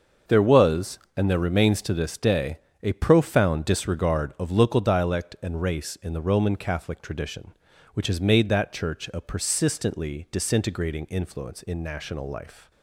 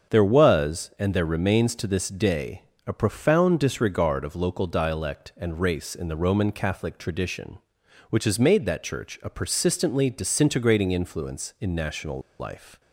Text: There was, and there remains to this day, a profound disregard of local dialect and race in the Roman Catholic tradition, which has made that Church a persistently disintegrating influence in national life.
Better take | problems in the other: first | starts louder than the rest; strong; until 1.1 s; 7 dB; also in the first // pauses between "national" and "life"; slight; at 12.2 s; 0.19 s long

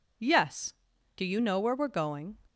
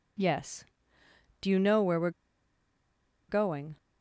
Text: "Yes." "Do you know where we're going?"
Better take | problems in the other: first | pauses between "we're" and "going"; at 2.0 s; 1.1 s long

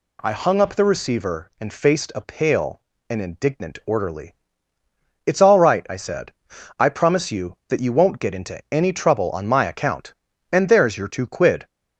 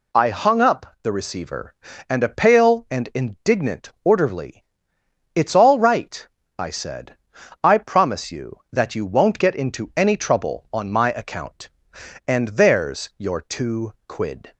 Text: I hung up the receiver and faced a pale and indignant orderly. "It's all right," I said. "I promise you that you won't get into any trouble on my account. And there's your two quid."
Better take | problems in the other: first | skips "faced"; at 2.2 s // pauses between "two" and "quid"; slight; at 13.9 s; 0.16 s long

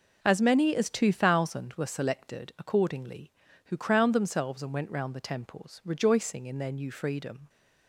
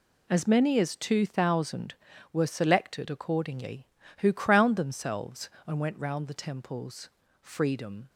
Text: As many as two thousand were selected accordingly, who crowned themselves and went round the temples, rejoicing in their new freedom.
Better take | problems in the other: first | skips "rejoicing in their new"; at 7.2 s

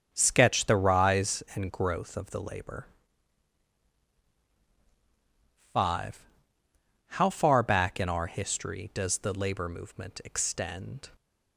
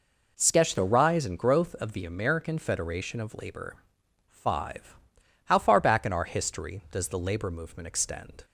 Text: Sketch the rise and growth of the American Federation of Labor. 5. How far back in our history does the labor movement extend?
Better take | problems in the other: second | starts louder than the rest; until 1.1 s; 7 dB // skips "American Federation of"; at 2.4 s

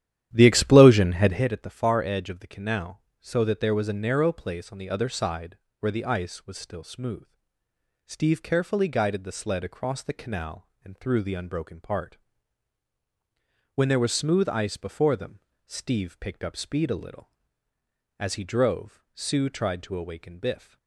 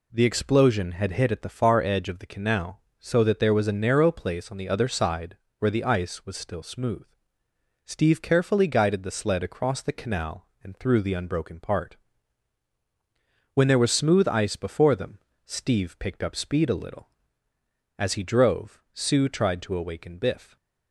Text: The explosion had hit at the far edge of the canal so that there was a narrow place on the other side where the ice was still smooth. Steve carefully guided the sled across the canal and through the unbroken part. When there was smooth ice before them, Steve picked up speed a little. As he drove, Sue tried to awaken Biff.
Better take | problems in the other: second | starts louder than the rest; strong; until 1.4 s; 11.5 dB // pauses between "side" and "where"; slight; at 5.5 s; 0.24 s long; slight in the second

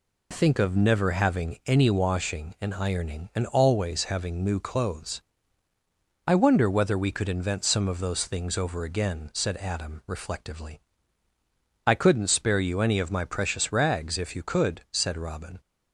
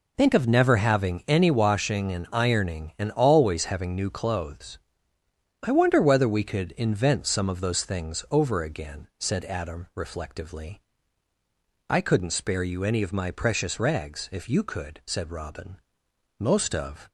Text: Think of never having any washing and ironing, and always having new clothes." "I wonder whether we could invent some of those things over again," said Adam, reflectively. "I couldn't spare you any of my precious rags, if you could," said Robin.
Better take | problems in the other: first | goes on to say "Most of"; noticeable; from 16.3 s on; 0.70 s long

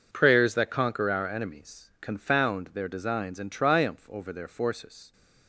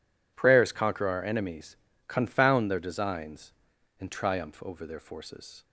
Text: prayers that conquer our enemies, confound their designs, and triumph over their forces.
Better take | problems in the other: first | skips "that"; at 0.7 s

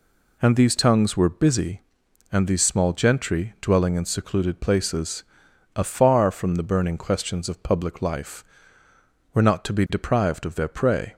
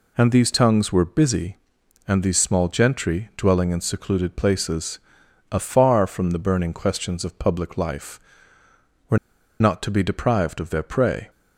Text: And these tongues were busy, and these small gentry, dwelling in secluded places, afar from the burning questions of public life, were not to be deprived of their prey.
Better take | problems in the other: first | pauses between "were" and "not"; at 9.1 s; 0.42 s long

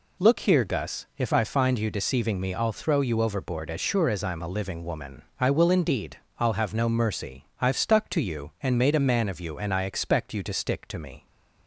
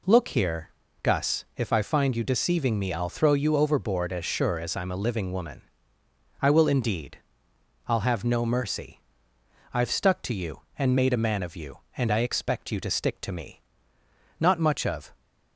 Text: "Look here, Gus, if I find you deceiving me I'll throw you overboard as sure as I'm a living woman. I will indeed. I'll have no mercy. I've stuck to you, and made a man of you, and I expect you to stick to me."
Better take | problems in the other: first | goes on to say "Not much of"; noticeable; from 14.3 s on; 0.76 s long

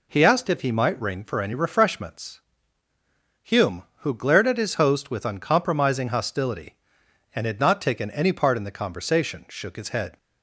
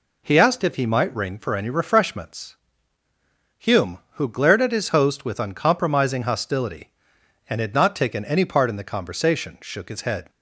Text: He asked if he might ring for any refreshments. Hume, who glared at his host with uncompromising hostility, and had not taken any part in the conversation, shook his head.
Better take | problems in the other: neither | none

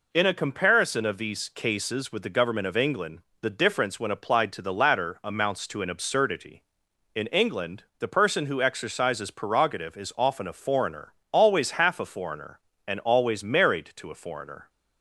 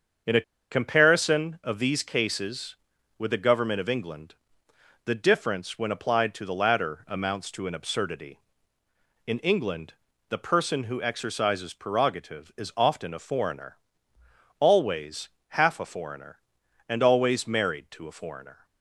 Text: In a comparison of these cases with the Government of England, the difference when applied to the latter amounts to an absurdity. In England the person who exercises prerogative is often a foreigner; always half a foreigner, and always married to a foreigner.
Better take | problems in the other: first | starts louder than the rest; until 1.5 s; 6.5 dB // pauses between "a" and "comparison"; slight; at 0.4 s; 0.29 s long // pauses between "England" and "the"; slight; at 9.9 s; 0.34 s long // pauses between "always" and "half"; slight; at 15.2 s; 0.22 s long

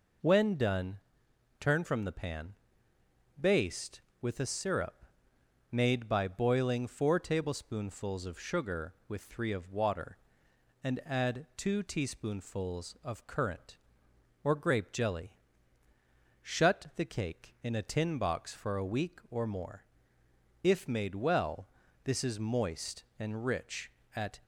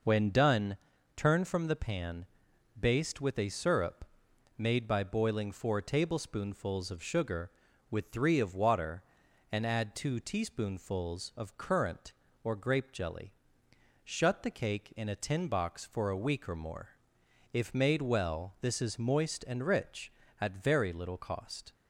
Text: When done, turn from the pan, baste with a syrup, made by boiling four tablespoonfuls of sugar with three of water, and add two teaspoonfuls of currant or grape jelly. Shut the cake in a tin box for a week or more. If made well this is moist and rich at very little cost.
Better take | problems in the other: second | pauses between "well" and "this"; at 21.6 s; 0.38 s long // stops before "very little cost"; at 24.4 s

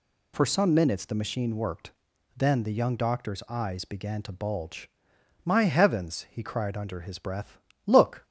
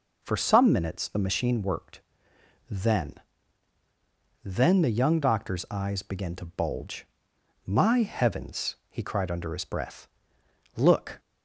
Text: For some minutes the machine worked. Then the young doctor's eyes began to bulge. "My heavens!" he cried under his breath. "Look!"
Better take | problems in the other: first | says "Then" twice; at 4.4 s

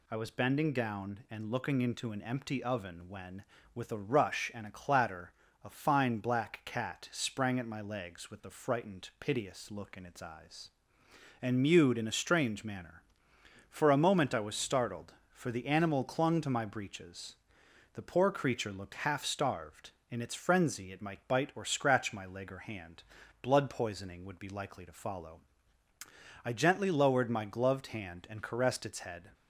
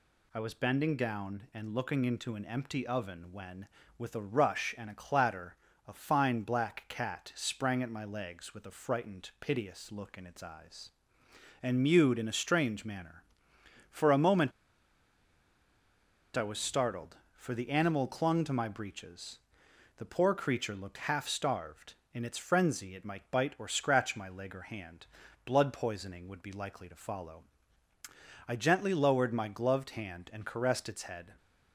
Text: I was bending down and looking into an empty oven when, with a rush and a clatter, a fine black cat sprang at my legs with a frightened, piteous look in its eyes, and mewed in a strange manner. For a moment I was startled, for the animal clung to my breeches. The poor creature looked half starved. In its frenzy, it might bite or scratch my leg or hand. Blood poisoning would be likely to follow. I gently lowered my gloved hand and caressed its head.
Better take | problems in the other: first | pauses between "moment" and "I"; strong; at 14.5 s; 1.8 s long

